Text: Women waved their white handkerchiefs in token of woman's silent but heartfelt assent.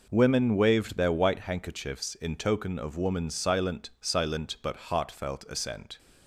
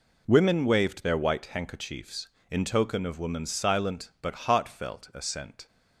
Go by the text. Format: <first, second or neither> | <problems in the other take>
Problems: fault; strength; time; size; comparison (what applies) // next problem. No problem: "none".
second | says "silent" twice; at 3.9 s